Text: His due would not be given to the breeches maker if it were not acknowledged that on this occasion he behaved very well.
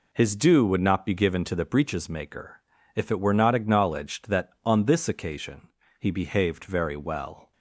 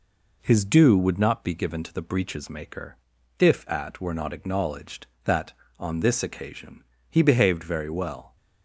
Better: first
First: pauses between "maker" and "if"; slight; at 2.6 s; 0.34 s long // pauses between "occasion" and "he"; slight; at 5.6 s; 0.32 s long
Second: pauses between "maker" and "if"; at 2.9 s; 0.44 s long // says "at" for "it"; at 3.6 s // pauses between "occasion" and "he"; slight; at 6.8 s; 0.28 s long

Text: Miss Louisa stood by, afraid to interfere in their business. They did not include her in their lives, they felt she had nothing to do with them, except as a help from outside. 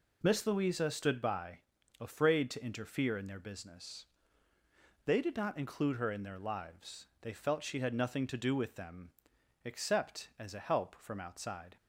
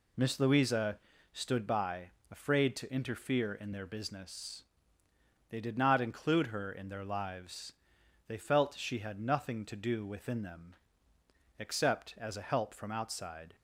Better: first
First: none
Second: pauses between "Louisa" and "stood"; slight; at 0.9 s; 0.34 s long // says "within" for "with"; at 10.0 s

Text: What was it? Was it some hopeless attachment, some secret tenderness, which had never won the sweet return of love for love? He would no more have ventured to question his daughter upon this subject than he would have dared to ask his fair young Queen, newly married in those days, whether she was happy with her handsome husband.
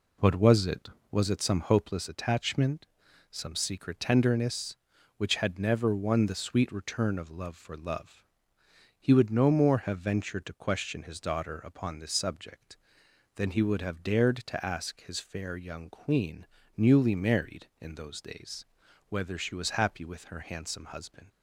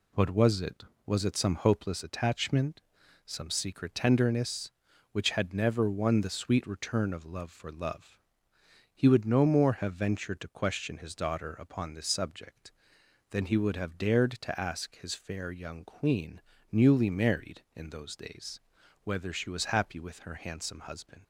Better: second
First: starts louder than the rest; until 1.3 s; 3.5 dB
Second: none

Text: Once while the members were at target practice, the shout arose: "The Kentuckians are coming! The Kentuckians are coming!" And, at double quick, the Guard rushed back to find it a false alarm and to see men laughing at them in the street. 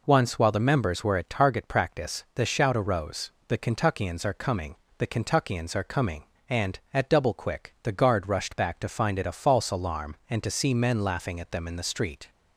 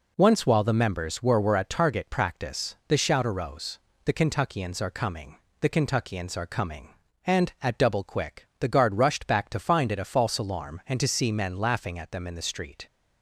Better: first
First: none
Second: says "were" twice; at 1.4 s

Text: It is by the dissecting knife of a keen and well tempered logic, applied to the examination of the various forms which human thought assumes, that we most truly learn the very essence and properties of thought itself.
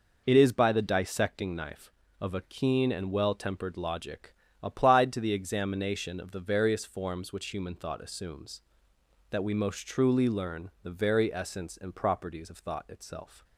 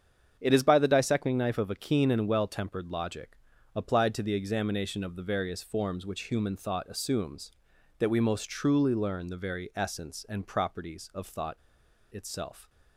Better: first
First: none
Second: starts louder than the rest; strong; until 1.4 s; 8 dB // pauses between "thought" and "itself"; noticeable; at 11.5 s; 0.55 s long

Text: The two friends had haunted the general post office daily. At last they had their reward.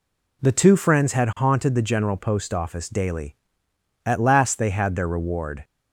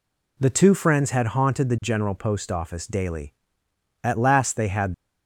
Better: first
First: none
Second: stops before "their reward"; at 4.9 s

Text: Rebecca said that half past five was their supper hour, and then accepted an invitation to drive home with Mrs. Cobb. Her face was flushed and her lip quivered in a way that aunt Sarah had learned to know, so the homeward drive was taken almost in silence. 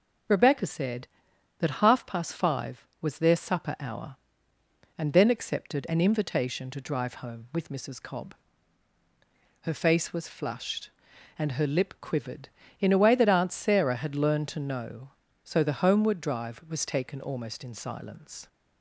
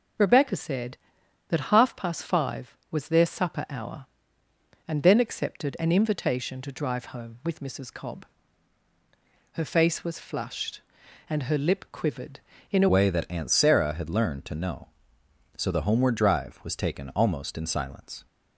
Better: first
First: none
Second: changes voice at "way"; from 12.8 s on; 5.4 s long

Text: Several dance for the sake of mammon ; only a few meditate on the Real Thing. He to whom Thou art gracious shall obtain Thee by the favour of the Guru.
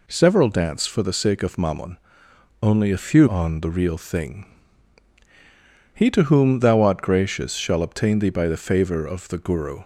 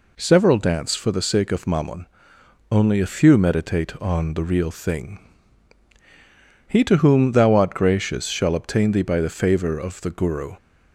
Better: second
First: skips "meditate"; at 3.2 s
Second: none

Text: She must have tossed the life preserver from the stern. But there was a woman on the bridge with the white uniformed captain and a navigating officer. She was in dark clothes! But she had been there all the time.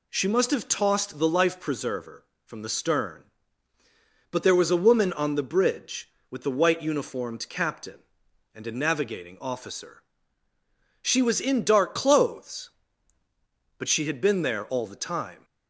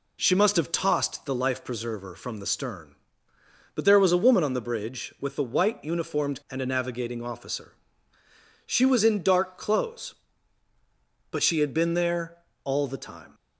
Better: first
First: none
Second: skips "captain"; at 6.4 s // pauses between "there" and "all"; slight; at 12.3 s; 0.26 s long

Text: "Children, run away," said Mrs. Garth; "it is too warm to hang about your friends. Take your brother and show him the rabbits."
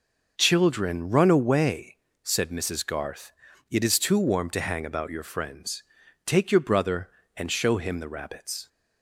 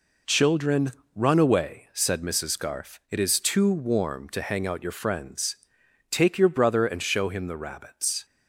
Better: first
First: none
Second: says "out" for "about"; at 4.6 s

